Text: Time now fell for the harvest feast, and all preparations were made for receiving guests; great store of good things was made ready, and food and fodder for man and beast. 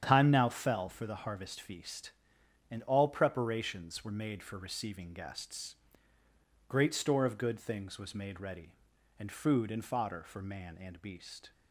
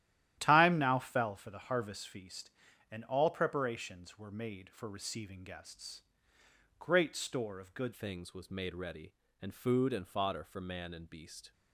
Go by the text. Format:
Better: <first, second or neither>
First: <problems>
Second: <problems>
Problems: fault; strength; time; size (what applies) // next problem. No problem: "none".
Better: first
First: starts louder than the rest; strong; until 1.0 s; 9 dB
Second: starts louder than the rest; strong; until 1.4 s; 12.5 dB // changes voice at "things"; from 7.9 s on; 3.6 s long